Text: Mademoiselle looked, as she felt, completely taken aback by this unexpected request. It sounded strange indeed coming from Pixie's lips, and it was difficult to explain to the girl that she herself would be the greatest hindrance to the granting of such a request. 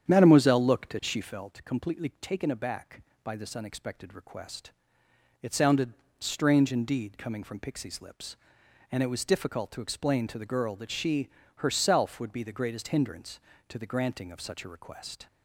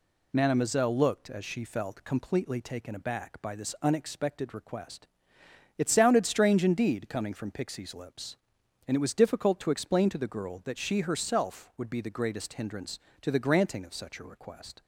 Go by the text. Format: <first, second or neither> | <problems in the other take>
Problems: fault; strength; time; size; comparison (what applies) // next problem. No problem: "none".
second | starts louder than the rest; strong; until 1.3 s; 9 dB // pauses between "sounded" and "strange"; slight; at 5.9 s; 0.26 s long // pauses between "she" and "herself"; slight; at 11.2 s; 0.28 s long